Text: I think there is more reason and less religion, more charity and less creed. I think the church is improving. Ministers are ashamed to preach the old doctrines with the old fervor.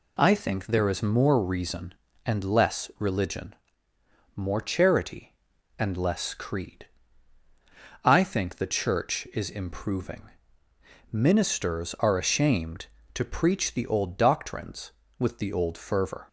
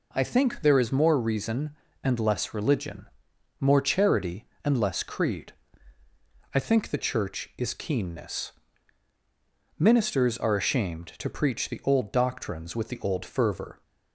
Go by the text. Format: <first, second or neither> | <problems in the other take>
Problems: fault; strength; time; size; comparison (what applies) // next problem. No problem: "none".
first | says "keenness" for "improving"; at 7.7 s